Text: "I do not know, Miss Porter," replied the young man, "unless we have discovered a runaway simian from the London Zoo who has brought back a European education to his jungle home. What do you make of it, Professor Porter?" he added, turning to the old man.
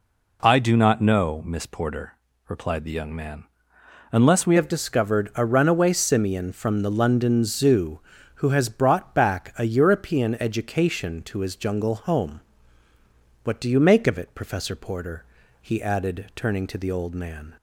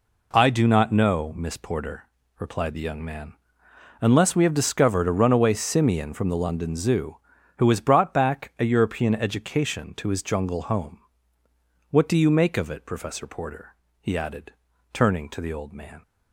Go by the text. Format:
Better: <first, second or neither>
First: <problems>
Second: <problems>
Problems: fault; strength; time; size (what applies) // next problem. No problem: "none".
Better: second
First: changes voice at "have"; from 4.5 s on; 13.0 s long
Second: none